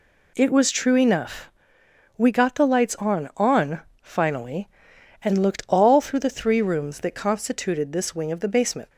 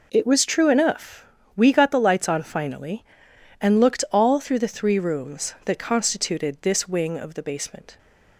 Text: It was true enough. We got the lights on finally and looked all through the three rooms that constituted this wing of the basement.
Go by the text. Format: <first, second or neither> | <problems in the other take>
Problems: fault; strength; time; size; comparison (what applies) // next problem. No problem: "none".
second | says "on" twice; at 3.3 s